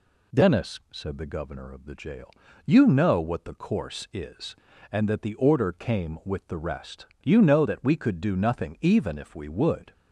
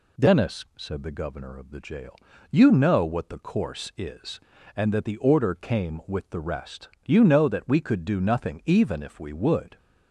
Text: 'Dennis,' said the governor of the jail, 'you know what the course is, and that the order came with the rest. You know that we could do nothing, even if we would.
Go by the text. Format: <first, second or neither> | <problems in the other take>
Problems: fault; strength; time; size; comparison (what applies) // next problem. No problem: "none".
neither | none